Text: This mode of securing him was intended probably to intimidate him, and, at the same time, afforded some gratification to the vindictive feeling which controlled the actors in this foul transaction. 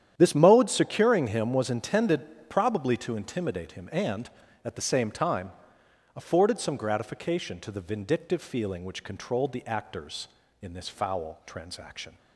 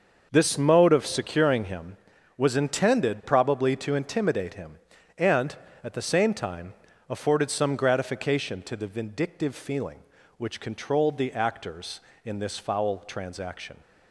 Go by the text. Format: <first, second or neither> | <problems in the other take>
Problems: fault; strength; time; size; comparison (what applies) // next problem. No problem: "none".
second | starts louder than the rest; strong; until 1.1 s; 10 dB; also in the second // skips "of"; at 0.6 s